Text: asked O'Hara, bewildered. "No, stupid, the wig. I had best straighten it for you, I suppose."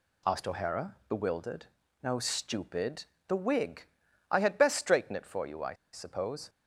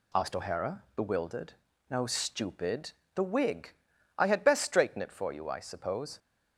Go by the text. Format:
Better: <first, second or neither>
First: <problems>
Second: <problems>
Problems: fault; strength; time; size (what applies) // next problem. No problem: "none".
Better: second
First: pauses between "I" and "suppose"; slight; at 5.7 s; 0.18 s long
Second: none